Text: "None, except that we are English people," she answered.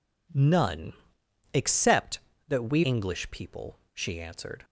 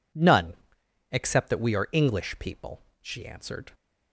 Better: second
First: skips "are"; at 2.8 s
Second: none

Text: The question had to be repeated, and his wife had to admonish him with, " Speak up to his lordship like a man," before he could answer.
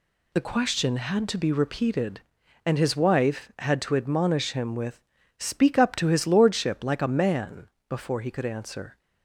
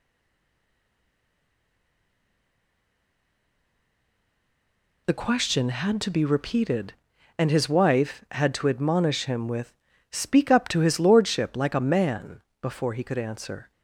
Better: first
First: none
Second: stays silent before the first word; strong; until 5.0 s; 5.0 s long

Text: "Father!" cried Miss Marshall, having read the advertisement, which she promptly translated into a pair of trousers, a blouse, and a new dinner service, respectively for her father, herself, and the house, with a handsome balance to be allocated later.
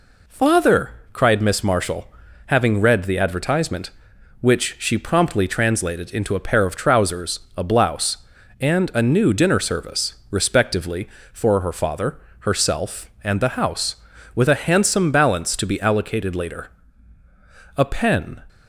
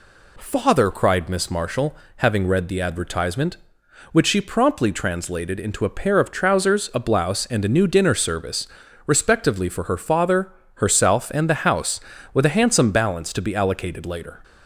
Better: second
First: goes on to say "A pen"; noticeable; from 17.7 s on; 0.64 s long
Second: none

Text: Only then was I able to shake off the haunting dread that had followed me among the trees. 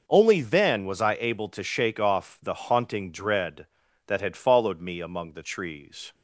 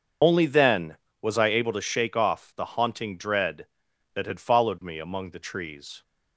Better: first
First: none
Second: loses the start of "Only"; at 0.2 s; 70 ms // starts louder than the rest; until 1.4 s; 7 dB

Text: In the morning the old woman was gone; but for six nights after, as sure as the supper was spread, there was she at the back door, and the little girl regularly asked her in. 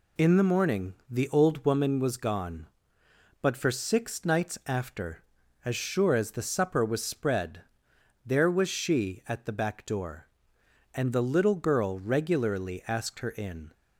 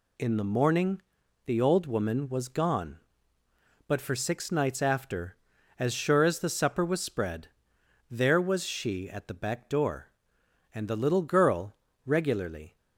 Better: first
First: pauses between "morning" and "the"; slight; at 0.9 s; 0.16 s long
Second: pauses between "morning" and "the"; noticeable; at 1.0 s; 0.46 s long // pauses between "girl" and "regularly"; slight; at 11.7 s; 0.28 s long // stops before "asked her in"; at 12.7 s

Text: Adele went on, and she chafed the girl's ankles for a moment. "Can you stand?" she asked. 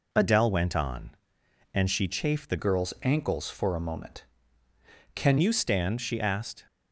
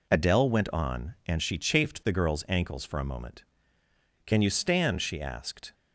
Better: second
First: changes voice from "girl's" to "Can"; from 2.5 to 5.3 s; 2.8 s long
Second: none

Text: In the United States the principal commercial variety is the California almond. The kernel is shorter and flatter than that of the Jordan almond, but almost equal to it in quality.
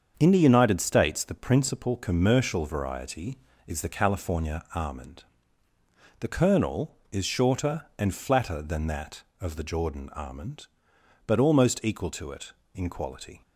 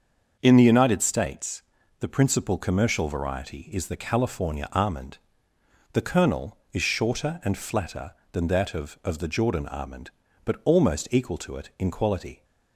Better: first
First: starts louder than the rest; strong; until 1.1 s; 7 dB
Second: starts louder than the rest; until 1.4 s; 6.5 dB // pauses between "States" and "the"; slight; at 1.6 s; 0.34 s long // says "of" twice; at 9.0 s

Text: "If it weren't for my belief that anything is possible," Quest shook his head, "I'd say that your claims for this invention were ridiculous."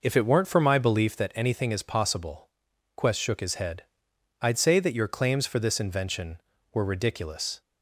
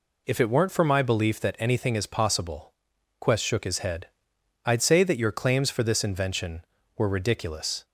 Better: second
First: starts louder than the rest; noticeable; until 1.2 s; 5 dB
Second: none

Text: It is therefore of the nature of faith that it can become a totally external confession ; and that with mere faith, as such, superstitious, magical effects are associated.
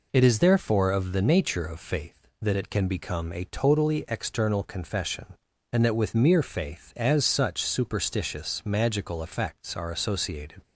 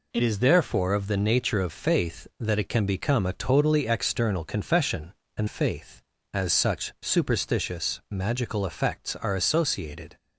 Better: first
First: none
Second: skips "that with mere"; at 5.4 s

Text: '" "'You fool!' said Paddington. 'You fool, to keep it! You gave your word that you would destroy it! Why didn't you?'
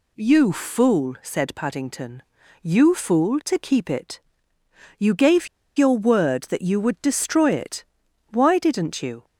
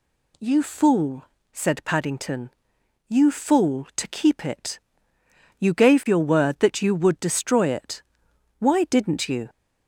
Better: second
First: pauses between "gave" and "your"; slight; at 5.4 s; 0.30 s long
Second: none

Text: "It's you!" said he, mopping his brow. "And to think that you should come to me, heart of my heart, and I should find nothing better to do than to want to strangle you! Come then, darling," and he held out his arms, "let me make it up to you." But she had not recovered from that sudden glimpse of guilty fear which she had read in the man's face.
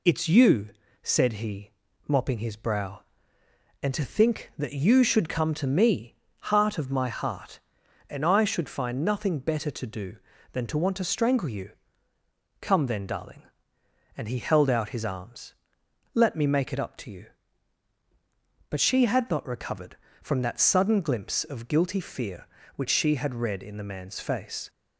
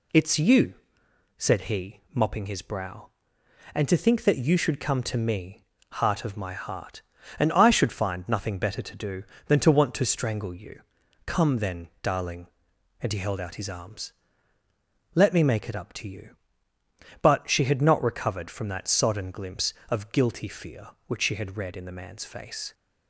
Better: first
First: none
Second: says "sodden" for "sudden"; at 18.8 s

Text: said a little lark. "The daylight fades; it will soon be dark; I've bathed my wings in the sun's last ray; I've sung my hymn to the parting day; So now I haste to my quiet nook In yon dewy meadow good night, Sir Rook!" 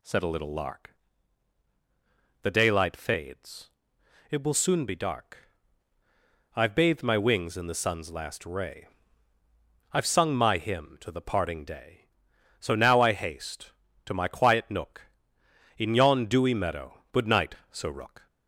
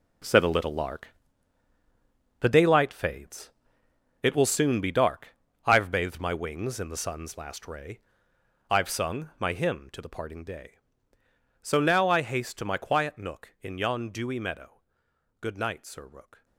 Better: first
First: none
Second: gets quieter; strong; throughout; 11.5 dB // pauses between "meadow" and "good"; noticeable; at 14.7 s; 0.62 s long

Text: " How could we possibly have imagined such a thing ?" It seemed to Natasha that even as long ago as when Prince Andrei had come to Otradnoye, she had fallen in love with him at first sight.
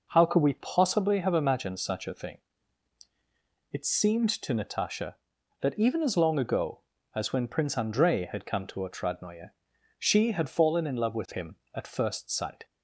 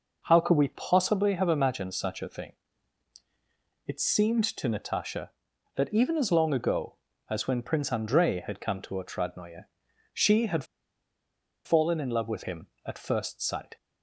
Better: first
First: none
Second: pauses between "had" and "fallen"; at 10.6 s; 1.0 s long

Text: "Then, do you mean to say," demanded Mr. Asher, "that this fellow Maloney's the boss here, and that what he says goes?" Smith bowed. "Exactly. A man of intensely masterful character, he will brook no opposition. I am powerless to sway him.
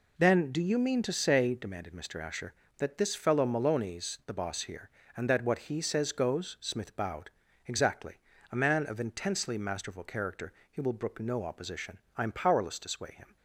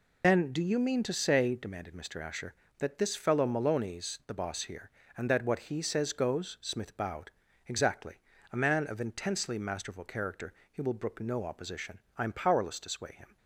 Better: first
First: none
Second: loses the start of "Then"; at 0.2 s; 60 ms

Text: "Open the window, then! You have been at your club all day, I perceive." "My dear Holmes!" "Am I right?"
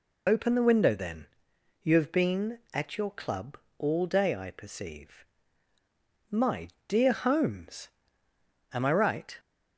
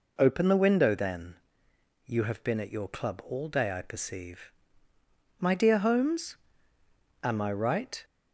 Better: second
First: loses the start of "Open"; at 0.2 s; 45 ms // pauses between "club" and "all"; slight; at 3.5 s; 0.20 s long // pauses between "My" and "dear"; slight; at 6.7 s; 0.18 s long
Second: none

